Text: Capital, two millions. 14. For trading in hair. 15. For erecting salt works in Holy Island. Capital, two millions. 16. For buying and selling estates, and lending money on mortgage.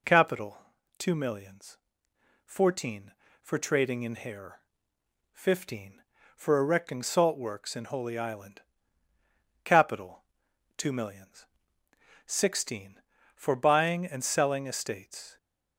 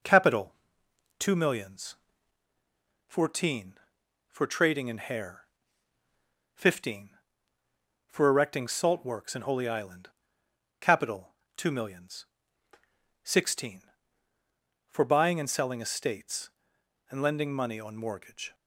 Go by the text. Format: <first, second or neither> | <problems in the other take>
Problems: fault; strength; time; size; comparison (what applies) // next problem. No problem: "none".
second | stops before "and lending money on mortgage"; at 15.3 s